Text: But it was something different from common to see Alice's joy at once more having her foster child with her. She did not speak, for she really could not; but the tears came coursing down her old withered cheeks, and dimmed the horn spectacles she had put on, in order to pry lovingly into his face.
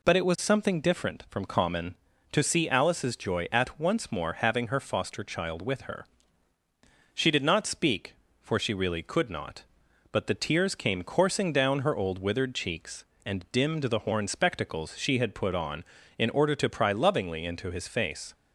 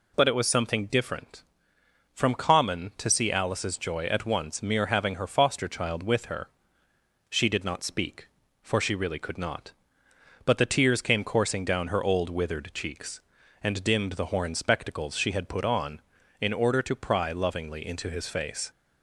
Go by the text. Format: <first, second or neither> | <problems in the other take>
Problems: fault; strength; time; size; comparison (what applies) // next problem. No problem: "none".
first | says "mere" for "more"; at 4.6 s